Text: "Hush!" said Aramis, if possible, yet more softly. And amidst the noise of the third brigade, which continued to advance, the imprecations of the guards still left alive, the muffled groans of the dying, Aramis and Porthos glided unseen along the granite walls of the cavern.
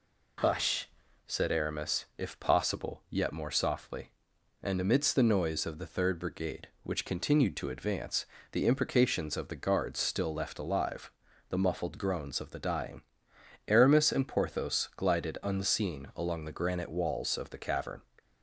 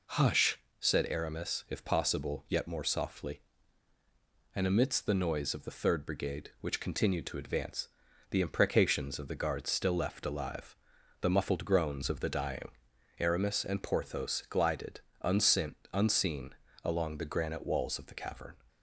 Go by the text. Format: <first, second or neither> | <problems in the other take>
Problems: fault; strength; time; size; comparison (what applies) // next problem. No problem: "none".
first | pauses between "glided" and "unseen"; slight; at 15.0 s; 0.20 s long // says "unseen" twice; at 15.9 s